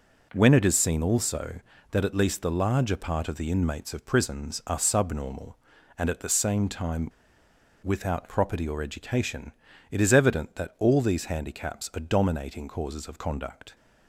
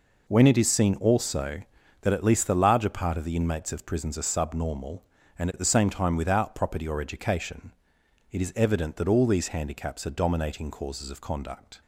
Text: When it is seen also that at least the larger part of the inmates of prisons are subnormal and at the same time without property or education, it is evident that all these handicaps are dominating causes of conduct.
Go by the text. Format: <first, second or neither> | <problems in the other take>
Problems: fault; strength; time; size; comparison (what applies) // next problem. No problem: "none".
second | pauses between "time" and "without"; noticeable; at 7.0 s; 0.76 s long